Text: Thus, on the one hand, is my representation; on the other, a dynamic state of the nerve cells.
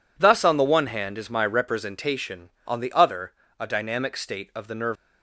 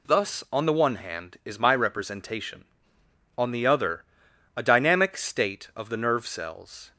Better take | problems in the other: second | stops before "cells"; at 4.9 s

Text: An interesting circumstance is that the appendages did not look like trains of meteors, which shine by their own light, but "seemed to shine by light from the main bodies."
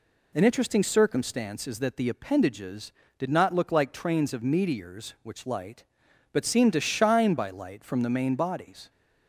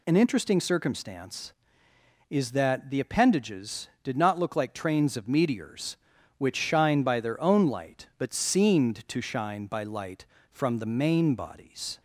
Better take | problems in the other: second | skips "shine by their own"; at 5.4 s

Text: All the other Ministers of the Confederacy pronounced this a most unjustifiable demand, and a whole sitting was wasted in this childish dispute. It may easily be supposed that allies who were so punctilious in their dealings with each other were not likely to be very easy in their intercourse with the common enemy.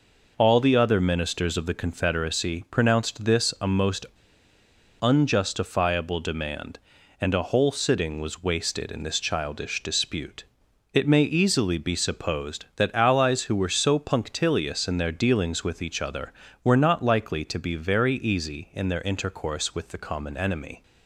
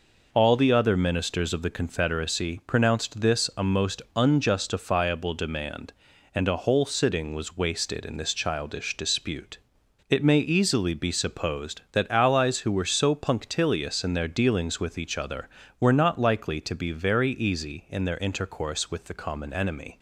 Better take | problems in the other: second | pauses between "most" and "unjustifiable"; noticeable; at 4.0 s; 0.96 s long

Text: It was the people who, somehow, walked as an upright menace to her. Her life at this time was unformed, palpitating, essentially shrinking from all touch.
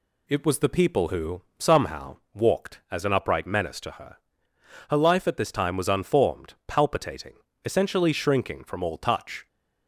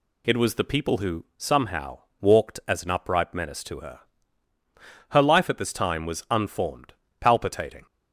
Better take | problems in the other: first | stops before "essentially shrinking from all touch"; at 7.8 s

